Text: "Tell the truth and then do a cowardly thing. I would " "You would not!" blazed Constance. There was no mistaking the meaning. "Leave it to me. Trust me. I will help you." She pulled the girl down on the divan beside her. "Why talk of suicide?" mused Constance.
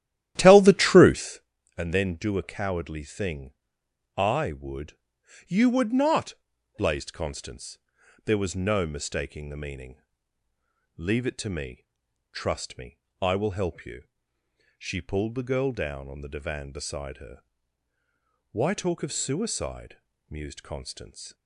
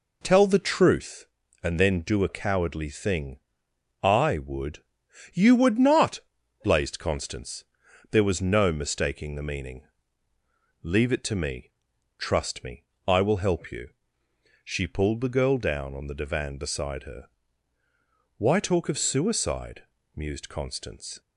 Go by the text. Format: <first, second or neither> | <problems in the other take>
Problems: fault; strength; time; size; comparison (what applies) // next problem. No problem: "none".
second | starts louder than the rest; strong; until 1.5 s; 12.5 dB